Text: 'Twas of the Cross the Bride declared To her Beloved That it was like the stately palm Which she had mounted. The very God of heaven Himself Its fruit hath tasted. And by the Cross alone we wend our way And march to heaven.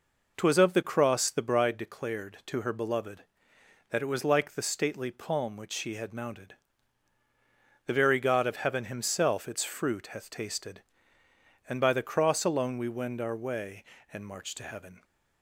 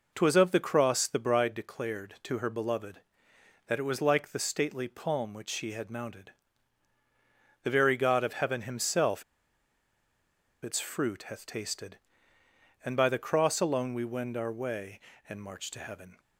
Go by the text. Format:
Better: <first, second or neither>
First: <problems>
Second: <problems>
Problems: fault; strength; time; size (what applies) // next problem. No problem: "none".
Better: first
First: none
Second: pauses between "Himself" and "Its"; strong; at 9.2 s; 1.4 s long